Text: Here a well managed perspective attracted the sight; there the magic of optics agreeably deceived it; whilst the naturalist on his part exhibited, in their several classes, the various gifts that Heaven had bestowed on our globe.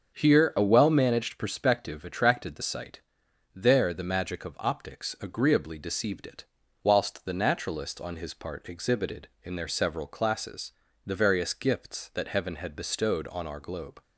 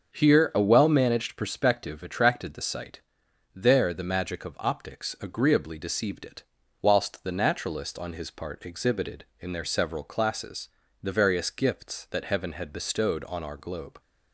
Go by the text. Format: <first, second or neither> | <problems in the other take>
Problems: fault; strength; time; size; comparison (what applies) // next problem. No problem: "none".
neither | starts louder than the rest; the same in both